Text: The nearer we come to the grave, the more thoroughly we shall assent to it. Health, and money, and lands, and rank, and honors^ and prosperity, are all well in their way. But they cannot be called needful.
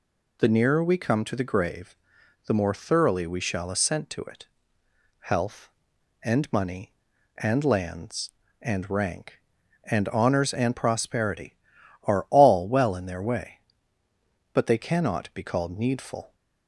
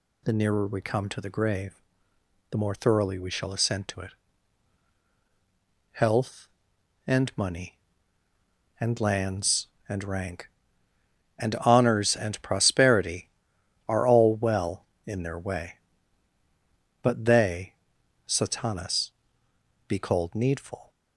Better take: first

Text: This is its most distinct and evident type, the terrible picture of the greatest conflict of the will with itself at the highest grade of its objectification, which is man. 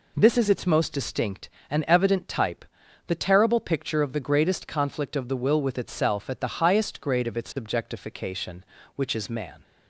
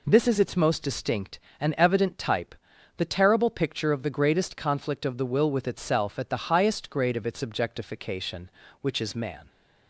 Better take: neither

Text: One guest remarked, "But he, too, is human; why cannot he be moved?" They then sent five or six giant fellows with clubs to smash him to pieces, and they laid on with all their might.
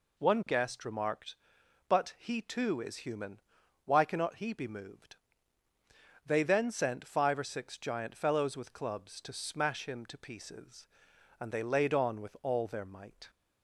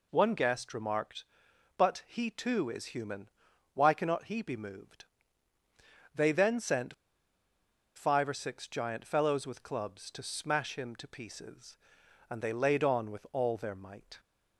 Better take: first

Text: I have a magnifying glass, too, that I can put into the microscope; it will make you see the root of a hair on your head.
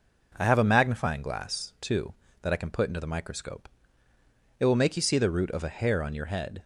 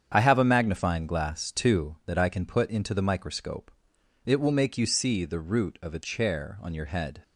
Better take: first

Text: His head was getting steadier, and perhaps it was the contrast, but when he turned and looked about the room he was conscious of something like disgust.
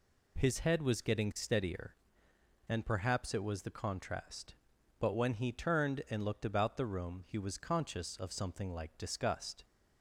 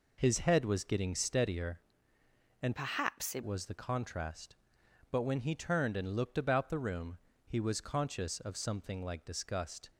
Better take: first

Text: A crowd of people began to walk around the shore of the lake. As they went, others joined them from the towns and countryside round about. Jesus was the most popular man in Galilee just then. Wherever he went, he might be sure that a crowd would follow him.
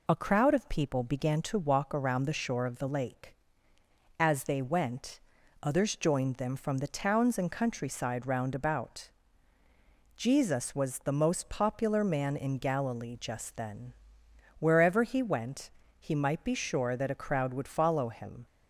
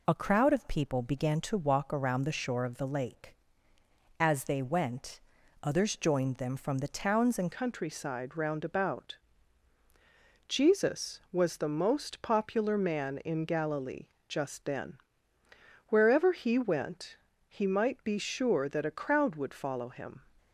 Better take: first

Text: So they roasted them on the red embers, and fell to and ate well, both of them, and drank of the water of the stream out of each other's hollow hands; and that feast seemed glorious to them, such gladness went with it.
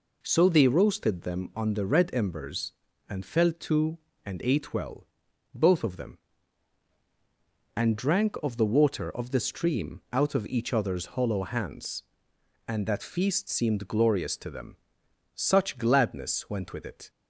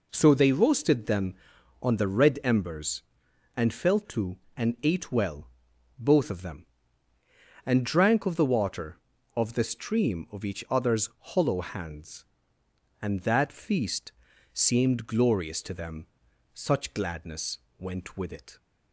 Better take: first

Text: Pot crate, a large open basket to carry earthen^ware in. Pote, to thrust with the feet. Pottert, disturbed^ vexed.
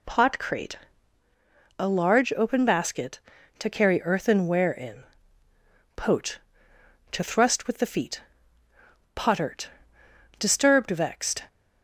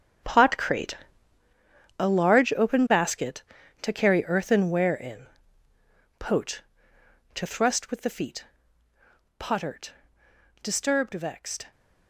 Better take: first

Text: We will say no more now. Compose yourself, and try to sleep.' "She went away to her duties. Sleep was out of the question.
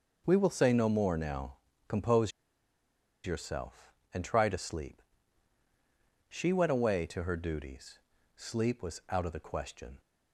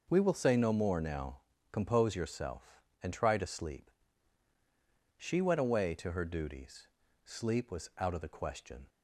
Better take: second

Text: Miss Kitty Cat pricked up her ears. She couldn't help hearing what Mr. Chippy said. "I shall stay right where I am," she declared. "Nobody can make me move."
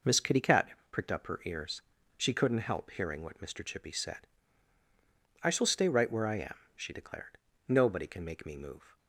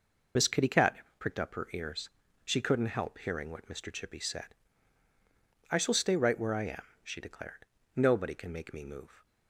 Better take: first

